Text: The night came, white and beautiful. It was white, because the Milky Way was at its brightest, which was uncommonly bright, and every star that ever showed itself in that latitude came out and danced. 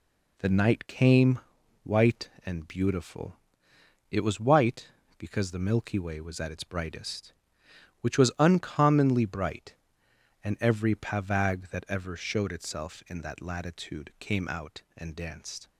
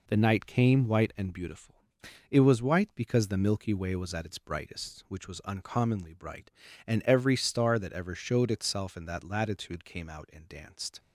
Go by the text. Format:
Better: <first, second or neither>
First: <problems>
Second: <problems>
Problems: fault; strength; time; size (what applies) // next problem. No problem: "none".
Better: second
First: says "pavag" for "star"; at 10.9 s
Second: none